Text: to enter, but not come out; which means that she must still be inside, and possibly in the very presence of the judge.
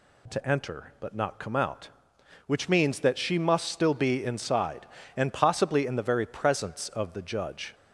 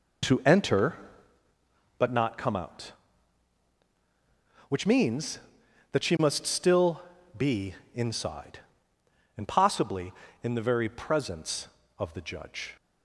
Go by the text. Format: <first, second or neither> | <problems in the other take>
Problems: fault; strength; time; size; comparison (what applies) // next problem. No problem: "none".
first | starts louder than the rest; noticeable; until 1.4 s; 4.5 dB // pauses between "still" and "be"; at 6.9 s; 0.38 s long // pauses between "be" and "inside"; slight; at 7.7 s; 0.18 s long